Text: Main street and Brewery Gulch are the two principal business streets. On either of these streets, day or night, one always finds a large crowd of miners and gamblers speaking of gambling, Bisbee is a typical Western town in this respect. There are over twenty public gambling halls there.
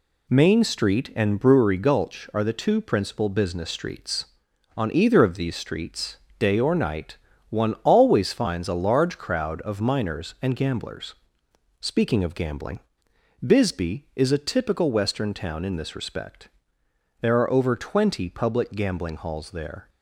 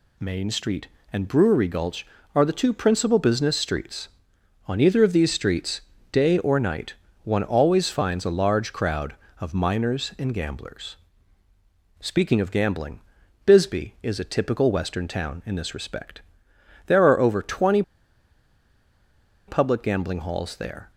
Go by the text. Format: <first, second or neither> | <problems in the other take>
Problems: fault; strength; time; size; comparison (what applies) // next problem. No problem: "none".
first | pauses between "gamblers" and "speaking"; at 10.9 s; 1.0 s long; noticeable in the first // pauses between "twenty" and "public"; strong; at 17.8 s; 1.6 s long